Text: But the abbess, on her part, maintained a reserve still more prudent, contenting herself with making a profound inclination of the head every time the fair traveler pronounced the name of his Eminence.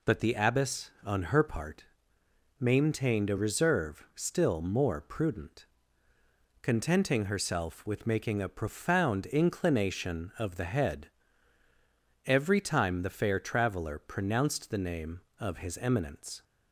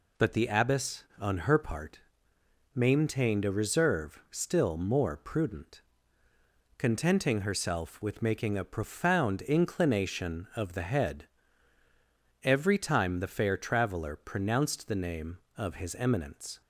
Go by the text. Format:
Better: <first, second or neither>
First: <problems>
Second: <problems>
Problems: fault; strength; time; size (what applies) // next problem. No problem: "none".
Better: neither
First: pauses between "head" and "every"; at 11.0 s; 1.1 s long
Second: pauses between "head" and "every"; at 11.2 s; 1.1 s long